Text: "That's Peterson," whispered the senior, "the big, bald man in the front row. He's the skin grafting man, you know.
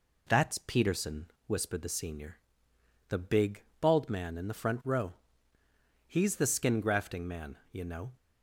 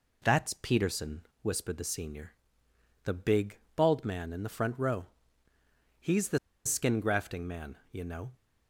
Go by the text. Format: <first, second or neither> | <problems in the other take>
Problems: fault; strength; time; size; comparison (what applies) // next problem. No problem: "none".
first | pauses between "the" and "skin"; slight; at 6.3 s; 0.27 s long